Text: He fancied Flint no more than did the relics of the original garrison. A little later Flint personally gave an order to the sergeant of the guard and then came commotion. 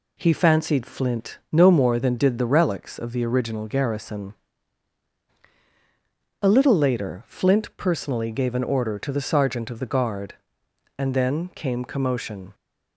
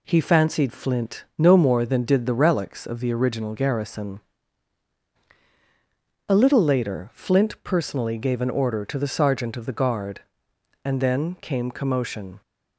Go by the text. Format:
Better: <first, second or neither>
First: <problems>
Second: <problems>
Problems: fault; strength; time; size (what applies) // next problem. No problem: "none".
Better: neither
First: none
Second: none